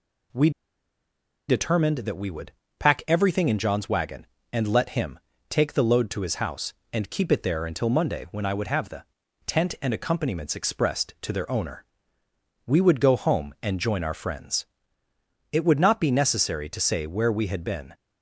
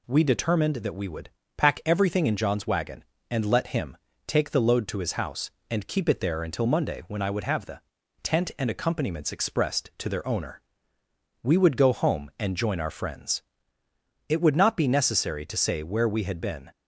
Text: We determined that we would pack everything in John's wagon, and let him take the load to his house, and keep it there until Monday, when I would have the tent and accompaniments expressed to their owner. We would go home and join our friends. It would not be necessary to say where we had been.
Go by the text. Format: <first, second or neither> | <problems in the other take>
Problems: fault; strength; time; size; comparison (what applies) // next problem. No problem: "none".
second | pauses between "We" and "determined"; at 0.5 s; 0.98 s long // pauses between "would" and "pack"; slight; at 2.5 s; 0.26 s long; slight in the second // pauses between "him" and "take"; slight; at 5.1 s; 0.32 s long; slight in the second // pauses between "the" and "tent"; at 9.0 s; 0.42 s long; also in the second